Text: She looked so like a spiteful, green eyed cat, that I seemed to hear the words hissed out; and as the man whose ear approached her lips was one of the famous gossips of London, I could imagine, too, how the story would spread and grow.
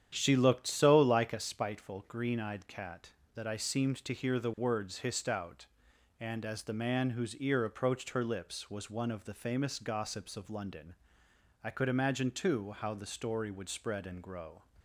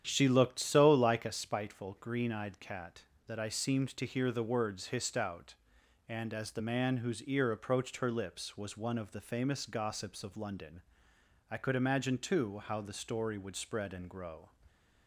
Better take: neither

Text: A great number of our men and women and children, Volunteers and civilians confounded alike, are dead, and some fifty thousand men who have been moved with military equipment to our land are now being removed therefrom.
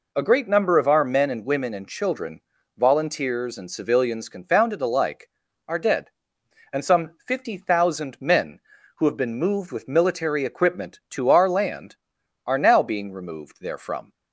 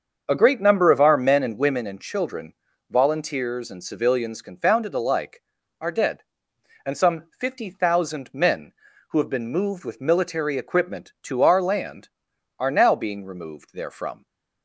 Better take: first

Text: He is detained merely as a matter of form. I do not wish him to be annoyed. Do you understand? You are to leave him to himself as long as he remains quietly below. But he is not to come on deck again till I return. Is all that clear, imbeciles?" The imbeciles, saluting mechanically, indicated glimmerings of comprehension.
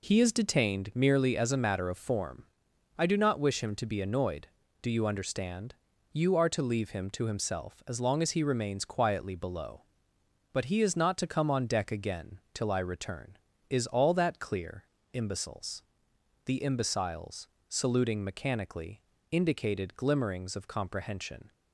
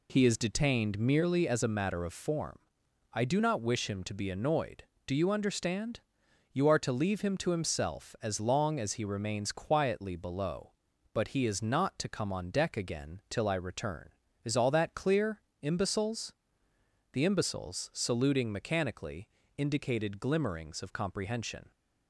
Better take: neither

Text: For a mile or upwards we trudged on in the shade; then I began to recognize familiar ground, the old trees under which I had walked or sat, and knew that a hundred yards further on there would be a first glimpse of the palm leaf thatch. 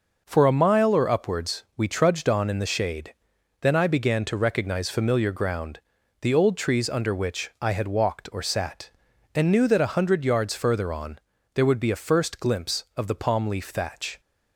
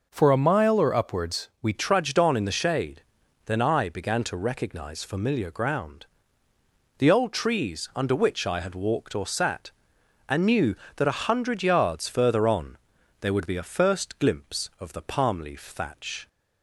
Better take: first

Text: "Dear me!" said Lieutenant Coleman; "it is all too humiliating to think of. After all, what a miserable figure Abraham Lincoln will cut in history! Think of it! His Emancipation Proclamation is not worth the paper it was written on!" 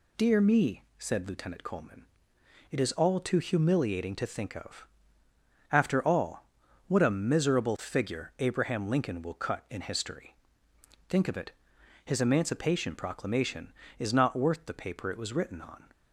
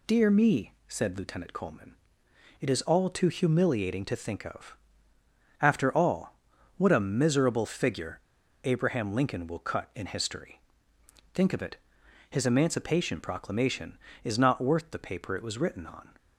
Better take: first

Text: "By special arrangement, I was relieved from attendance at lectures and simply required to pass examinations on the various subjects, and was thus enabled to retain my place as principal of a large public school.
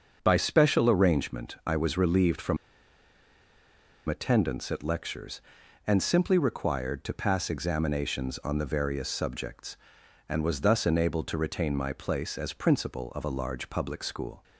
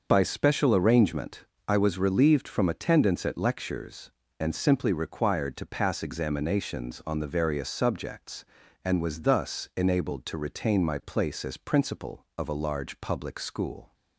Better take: second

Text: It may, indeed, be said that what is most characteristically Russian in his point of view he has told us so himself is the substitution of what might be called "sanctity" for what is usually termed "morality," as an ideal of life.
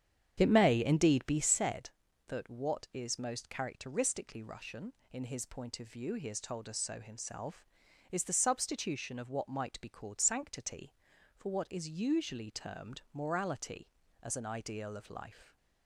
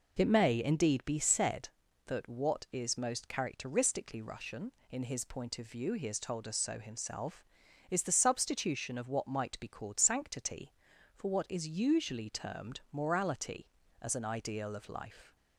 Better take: second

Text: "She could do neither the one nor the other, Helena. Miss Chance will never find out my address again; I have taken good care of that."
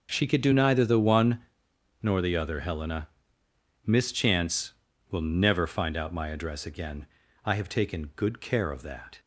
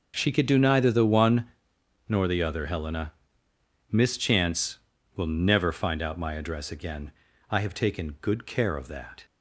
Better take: neither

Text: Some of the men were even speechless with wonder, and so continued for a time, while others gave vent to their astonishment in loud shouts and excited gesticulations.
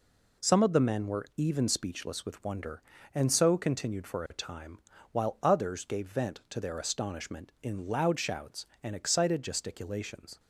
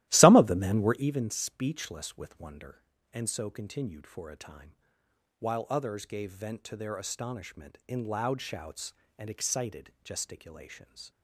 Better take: first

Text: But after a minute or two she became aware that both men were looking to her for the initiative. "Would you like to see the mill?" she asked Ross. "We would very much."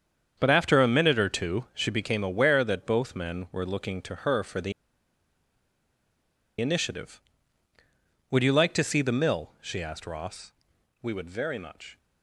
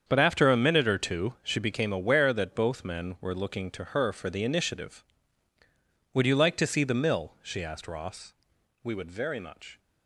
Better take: second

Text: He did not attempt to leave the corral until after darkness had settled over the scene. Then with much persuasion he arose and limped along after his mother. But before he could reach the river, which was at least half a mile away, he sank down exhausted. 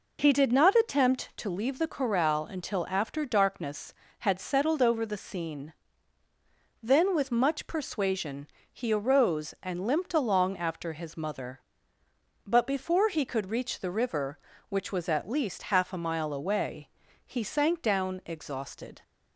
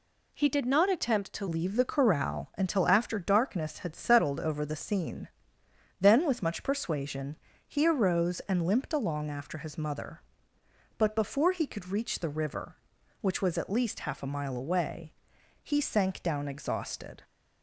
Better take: first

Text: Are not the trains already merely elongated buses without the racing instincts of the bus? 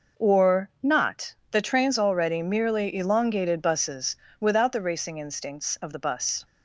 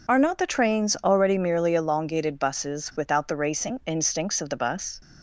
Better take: second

